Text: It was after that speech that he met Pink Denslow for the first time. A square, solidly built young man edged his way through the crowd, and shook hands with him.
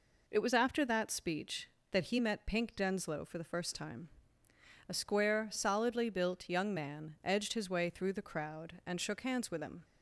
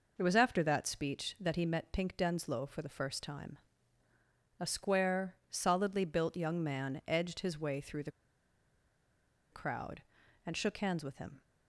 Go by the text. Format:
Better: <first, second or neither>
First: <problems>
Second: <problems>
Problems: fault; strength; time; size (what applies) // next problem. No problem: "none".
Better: first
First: none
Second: pauses between "the" and "crowd"; strong; at 8.1 s; 1.4 s long